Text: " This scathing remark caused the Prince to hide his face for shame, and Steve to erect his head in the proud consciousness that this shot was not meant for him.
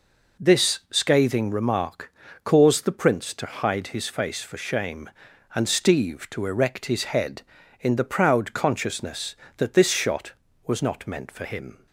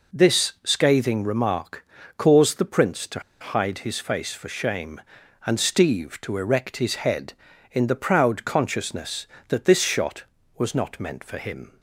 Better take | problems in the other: first | pauses between "remark" and "caused"; slight; at 1.8 s; 0.30 s long; slight in the first // pauses between "to" and "hide"; slight; at 3.1 s; 0.20 s long

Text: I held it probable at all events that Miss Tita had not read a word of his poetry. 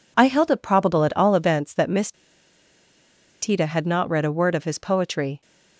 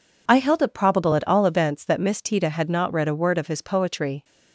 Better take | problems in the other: second | pauses between "Miss" and "Tita"; strong; at 2.1 s; 1.2 s long

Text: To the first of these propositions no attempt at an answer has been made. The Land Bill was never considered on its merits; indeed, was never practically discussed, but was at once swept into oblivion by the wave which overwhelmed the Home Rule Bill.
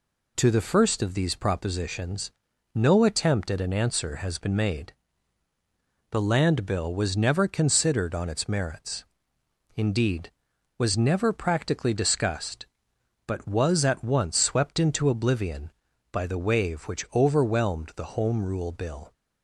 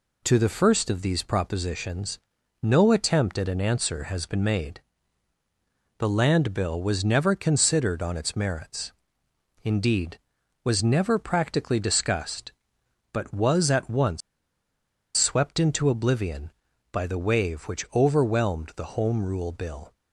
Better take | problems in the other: first | pauses between "propositions" and "no"; noticeable; at 2.1 s; 0.46 s long; noticeable in the first // pauses between "once" and "swept"; noticeable; at 14.2 s; 0.96 s long

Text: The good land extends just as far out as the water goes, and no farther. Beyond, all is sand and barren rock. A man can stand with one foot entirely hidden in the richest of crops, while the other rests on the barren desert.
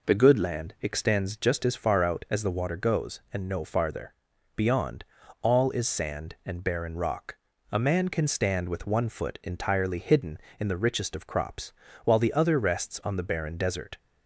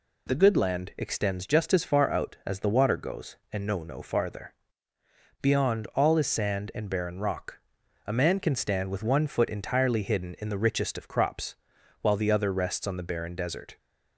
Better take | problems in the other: first | says "no" twice; at 3.8 s

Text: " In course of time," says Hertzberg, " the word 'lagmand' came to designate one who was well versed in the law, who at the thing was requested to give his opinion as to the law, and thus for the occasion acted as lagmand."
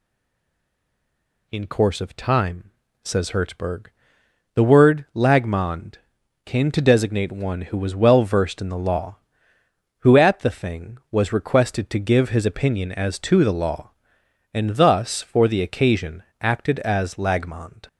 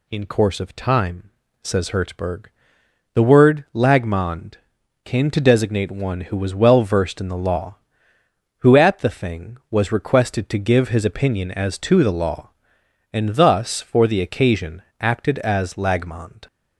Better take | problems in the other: second | stays silent before the first word; noticeable; until 1.4 s; 1.4 s long // pauses between "lagmand" and "came"; noticeable; at 5.9 s; 0.48 s long; noticeable in the second // pauses between "occasion" and "acted"; slight; at 16.2 s; 0.16 s long; slight in the second

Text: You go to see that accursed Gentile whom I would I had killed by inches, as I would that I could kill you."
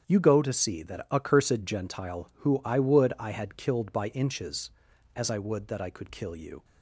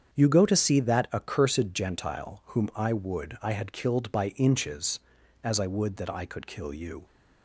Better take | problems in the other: second | starts louder than the rest; strong; until 1.0 s; 8 dB; strong in the second // says "who" for "whom"; at 2.4 s

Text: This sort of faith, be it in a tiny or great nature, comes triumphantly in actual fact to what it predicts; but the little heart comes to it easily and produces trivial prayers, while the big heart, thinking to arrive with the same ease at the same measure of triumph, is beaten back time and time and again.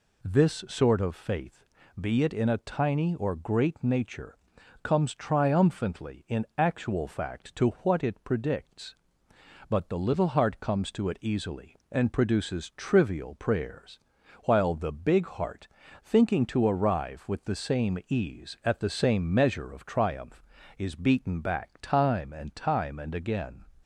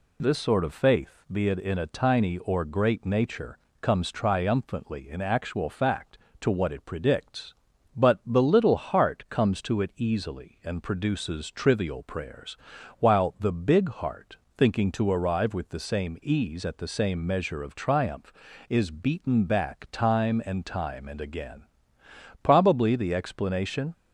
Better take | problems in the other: first | goes on to say "Probably the explanation"; from 22.4 s on; 1.5 s long

